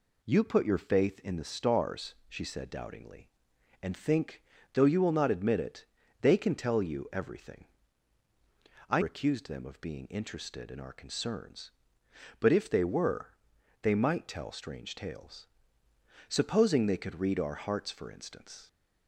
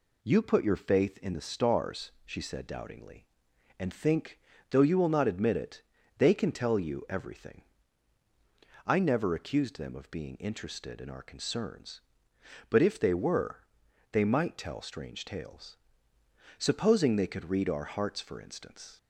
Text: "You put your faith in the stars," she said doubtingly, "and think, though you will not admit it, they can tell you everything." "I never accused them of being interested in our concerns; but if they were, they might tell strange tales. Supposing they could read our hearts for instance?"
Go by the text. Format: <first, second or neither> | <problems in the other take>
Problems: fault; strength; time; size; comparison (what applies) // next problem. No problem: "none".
second | skips "never"; at 9.0 s